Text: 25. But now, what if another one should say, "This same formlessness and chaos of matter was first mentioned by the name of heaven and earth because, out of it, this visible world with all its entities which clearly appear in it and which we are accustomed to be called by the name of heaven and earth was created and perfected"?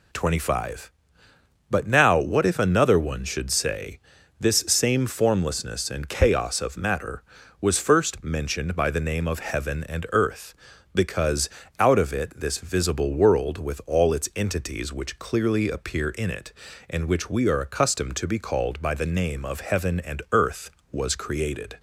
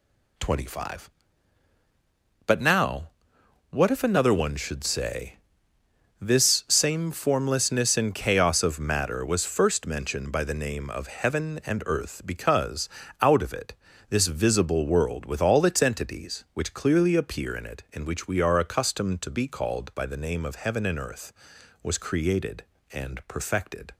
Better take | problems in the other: second | stops before "and perfected"; at 21.7 s

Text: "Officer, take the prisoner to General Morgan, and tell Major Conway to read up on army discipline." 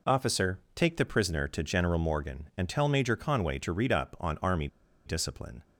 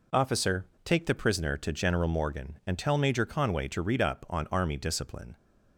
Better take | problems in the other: second | pauses between "army" and "discipline"; at 4.6 s; 0.39 s long

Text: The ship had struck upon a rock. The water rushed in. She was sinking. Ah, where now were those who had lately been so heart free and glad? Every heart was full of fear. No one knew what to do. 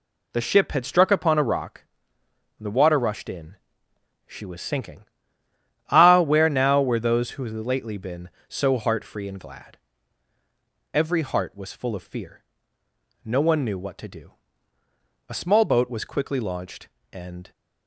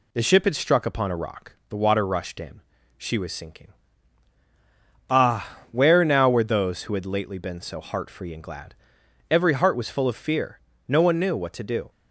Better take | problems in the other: second | goes on to say "A small boat was quickly launched and"; strong; from 15.2 s on; 2.2 s long

